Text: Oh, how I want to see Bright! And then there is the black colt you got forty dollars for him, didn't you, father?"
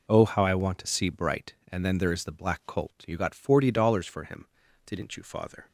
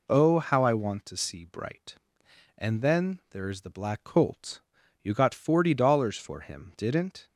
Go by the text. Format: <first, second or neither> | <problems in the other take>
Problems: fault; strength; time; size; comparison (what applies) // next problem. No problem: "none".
first | pauses between "colt" and "you"; at 4.6 s; 0.40 s long // stops before "you father"; at 7.2 s